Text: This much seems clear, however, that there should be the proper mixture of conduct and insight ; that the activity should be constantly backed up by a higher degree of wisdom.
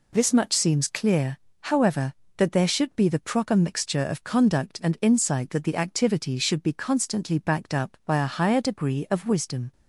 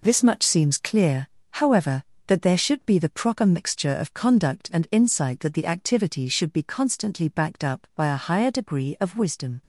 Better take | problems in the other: first | gets quieter; strong; throughout; 8.5 dB

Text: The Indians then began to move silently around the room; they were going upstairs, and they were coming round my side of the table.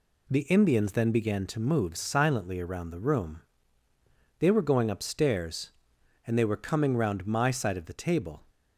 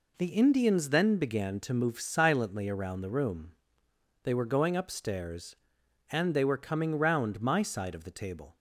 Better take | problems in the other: neither | none

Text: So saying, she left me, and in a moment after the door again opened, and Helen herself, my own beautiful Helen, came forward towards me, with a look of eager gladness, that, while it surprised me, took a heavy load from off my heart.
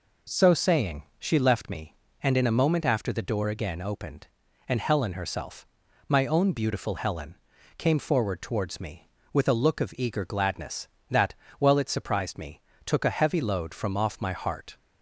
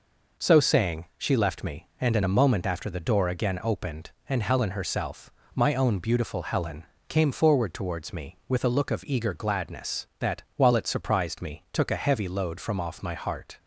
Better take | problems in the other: neither | none

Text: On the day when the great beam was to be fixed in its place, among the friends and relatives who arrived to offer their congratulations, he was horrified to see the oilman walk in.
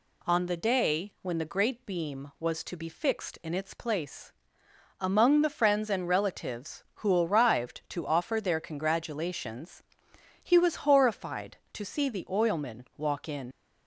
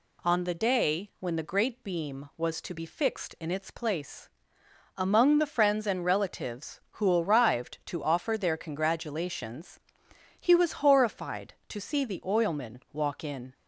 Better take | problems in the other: second | leaves "in" unfinished; at 13.5 s; 65 ms

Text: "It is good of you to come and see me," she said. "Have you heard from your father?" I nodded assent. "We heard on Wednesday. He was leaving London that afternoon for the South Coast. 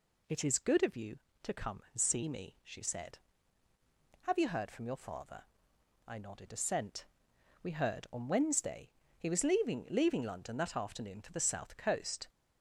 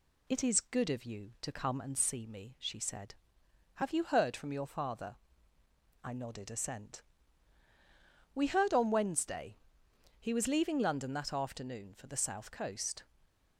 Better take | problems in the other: second | says "leaving" twice; at 9.9 s

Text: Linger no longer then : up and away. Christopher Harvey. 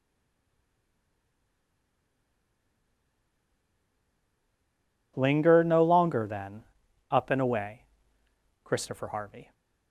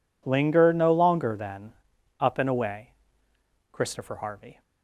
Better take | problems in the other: second | stays silent before the first word; strong; until 5.1 s; 5.1 s long

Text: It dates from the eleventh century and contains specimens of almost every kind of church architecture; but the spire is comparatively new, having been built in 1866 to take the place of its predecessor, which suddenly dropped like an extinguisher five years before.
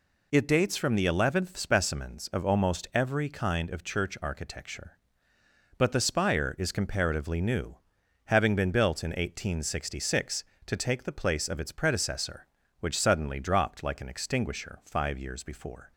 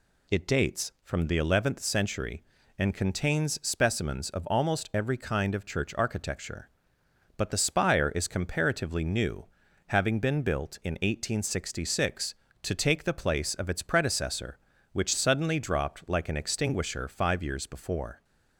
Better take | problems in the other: second | skips "century and contains"; at 1.5 s

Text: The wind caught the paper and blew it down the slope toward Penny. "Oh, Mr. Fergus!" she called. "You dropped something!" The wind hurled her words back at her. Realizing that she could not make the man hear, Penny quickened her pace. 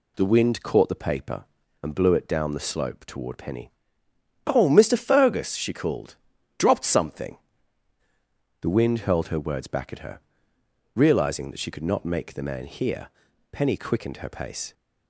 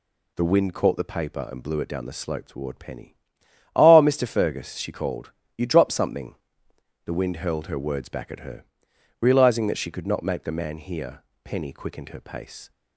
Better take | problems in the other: second | skips "You"; at 6.3 s

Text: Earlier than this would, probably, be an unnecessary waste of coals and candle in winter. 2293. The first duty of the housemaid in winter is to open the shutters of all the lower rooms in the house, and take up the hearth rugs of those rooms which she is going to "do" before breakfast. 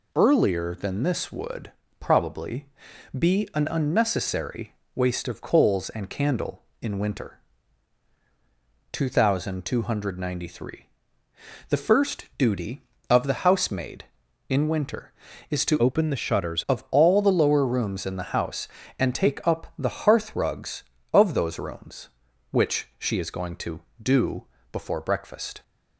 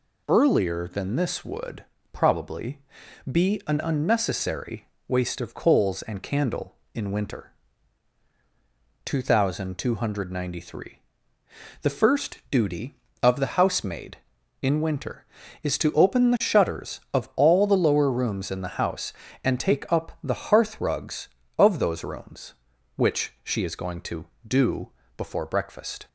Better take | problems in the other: second | pauses between "unnecessary" and "waste"; slight; at 4.7 s; 0.20 s long; slight in the second // changes voice from "open" to "shutters"; from 15.8 to 16.6 s; 0.8 s long // pauses between "do" and "before"; slight; at 24.4 s; 0.26 s long; slight in the second

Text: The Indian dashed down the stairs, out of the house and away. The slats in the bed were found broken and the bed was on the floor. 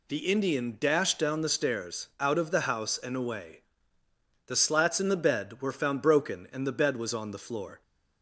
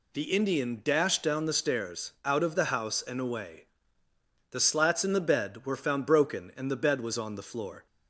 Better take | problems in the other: neither | none

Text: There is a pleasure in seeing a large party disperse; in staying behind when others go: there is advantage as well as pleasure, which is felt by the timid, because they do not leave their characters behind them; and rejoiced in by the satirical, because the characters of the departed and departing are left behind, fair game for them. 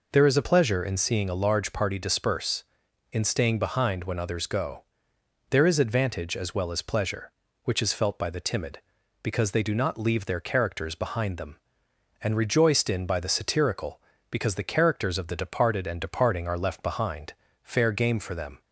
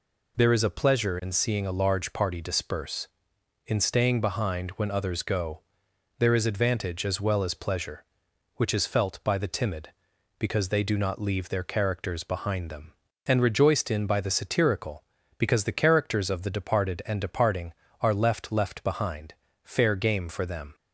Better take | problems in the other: first | says "left" twice; at 18.5 s

